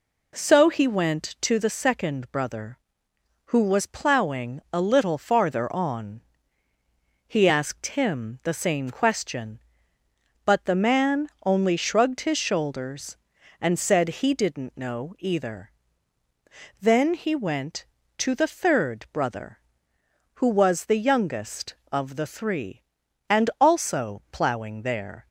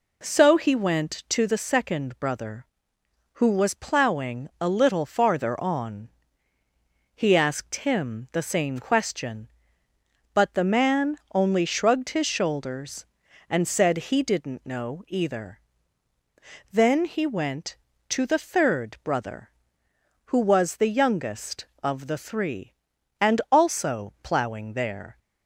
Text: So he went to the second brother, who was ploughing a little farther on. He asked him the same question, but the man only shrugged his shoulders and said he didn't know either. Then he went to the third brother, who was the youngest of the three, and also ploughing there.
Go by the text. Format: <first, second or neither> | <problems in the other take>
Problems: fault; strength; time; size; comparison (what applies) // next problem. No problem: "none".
neither | pauses between "man" and "only"; slight; the same in both